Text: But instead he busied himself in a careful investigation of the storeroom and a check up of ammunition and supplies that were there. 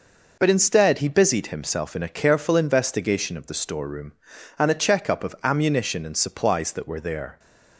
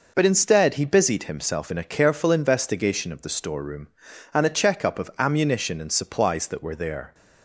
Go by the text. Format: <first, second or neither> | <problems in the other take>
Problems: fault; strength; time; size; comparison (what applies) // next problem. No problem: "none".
neither | none